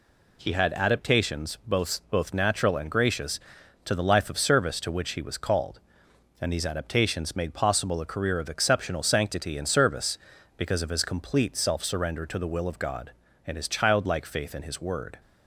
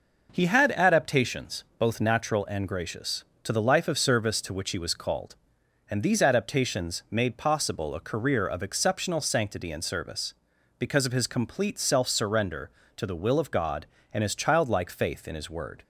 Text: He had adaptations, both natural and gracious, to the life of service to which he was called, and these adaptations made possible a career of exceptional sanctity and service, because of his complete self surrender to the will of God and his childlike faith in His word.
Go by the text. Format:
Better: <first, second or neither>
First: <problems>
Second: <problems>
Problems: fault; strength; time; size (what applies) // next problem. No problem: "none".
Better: second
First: says "both" twice; at 2.1 s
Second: none